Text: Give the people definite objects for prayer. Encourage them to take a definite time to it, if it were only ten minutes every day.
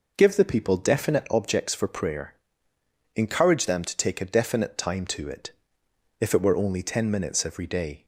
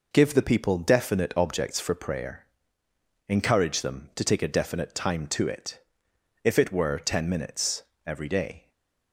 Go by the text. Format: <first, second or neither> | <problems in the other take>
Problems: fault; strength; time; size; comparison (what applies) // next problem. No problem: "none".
first | skips "only"; at 6.9 s // pauses between "minutes" and "every"; slight; at 7.8 s; 0.22 s long // stays silent after the last word; slight; from 8.5 s on; 0.6 s long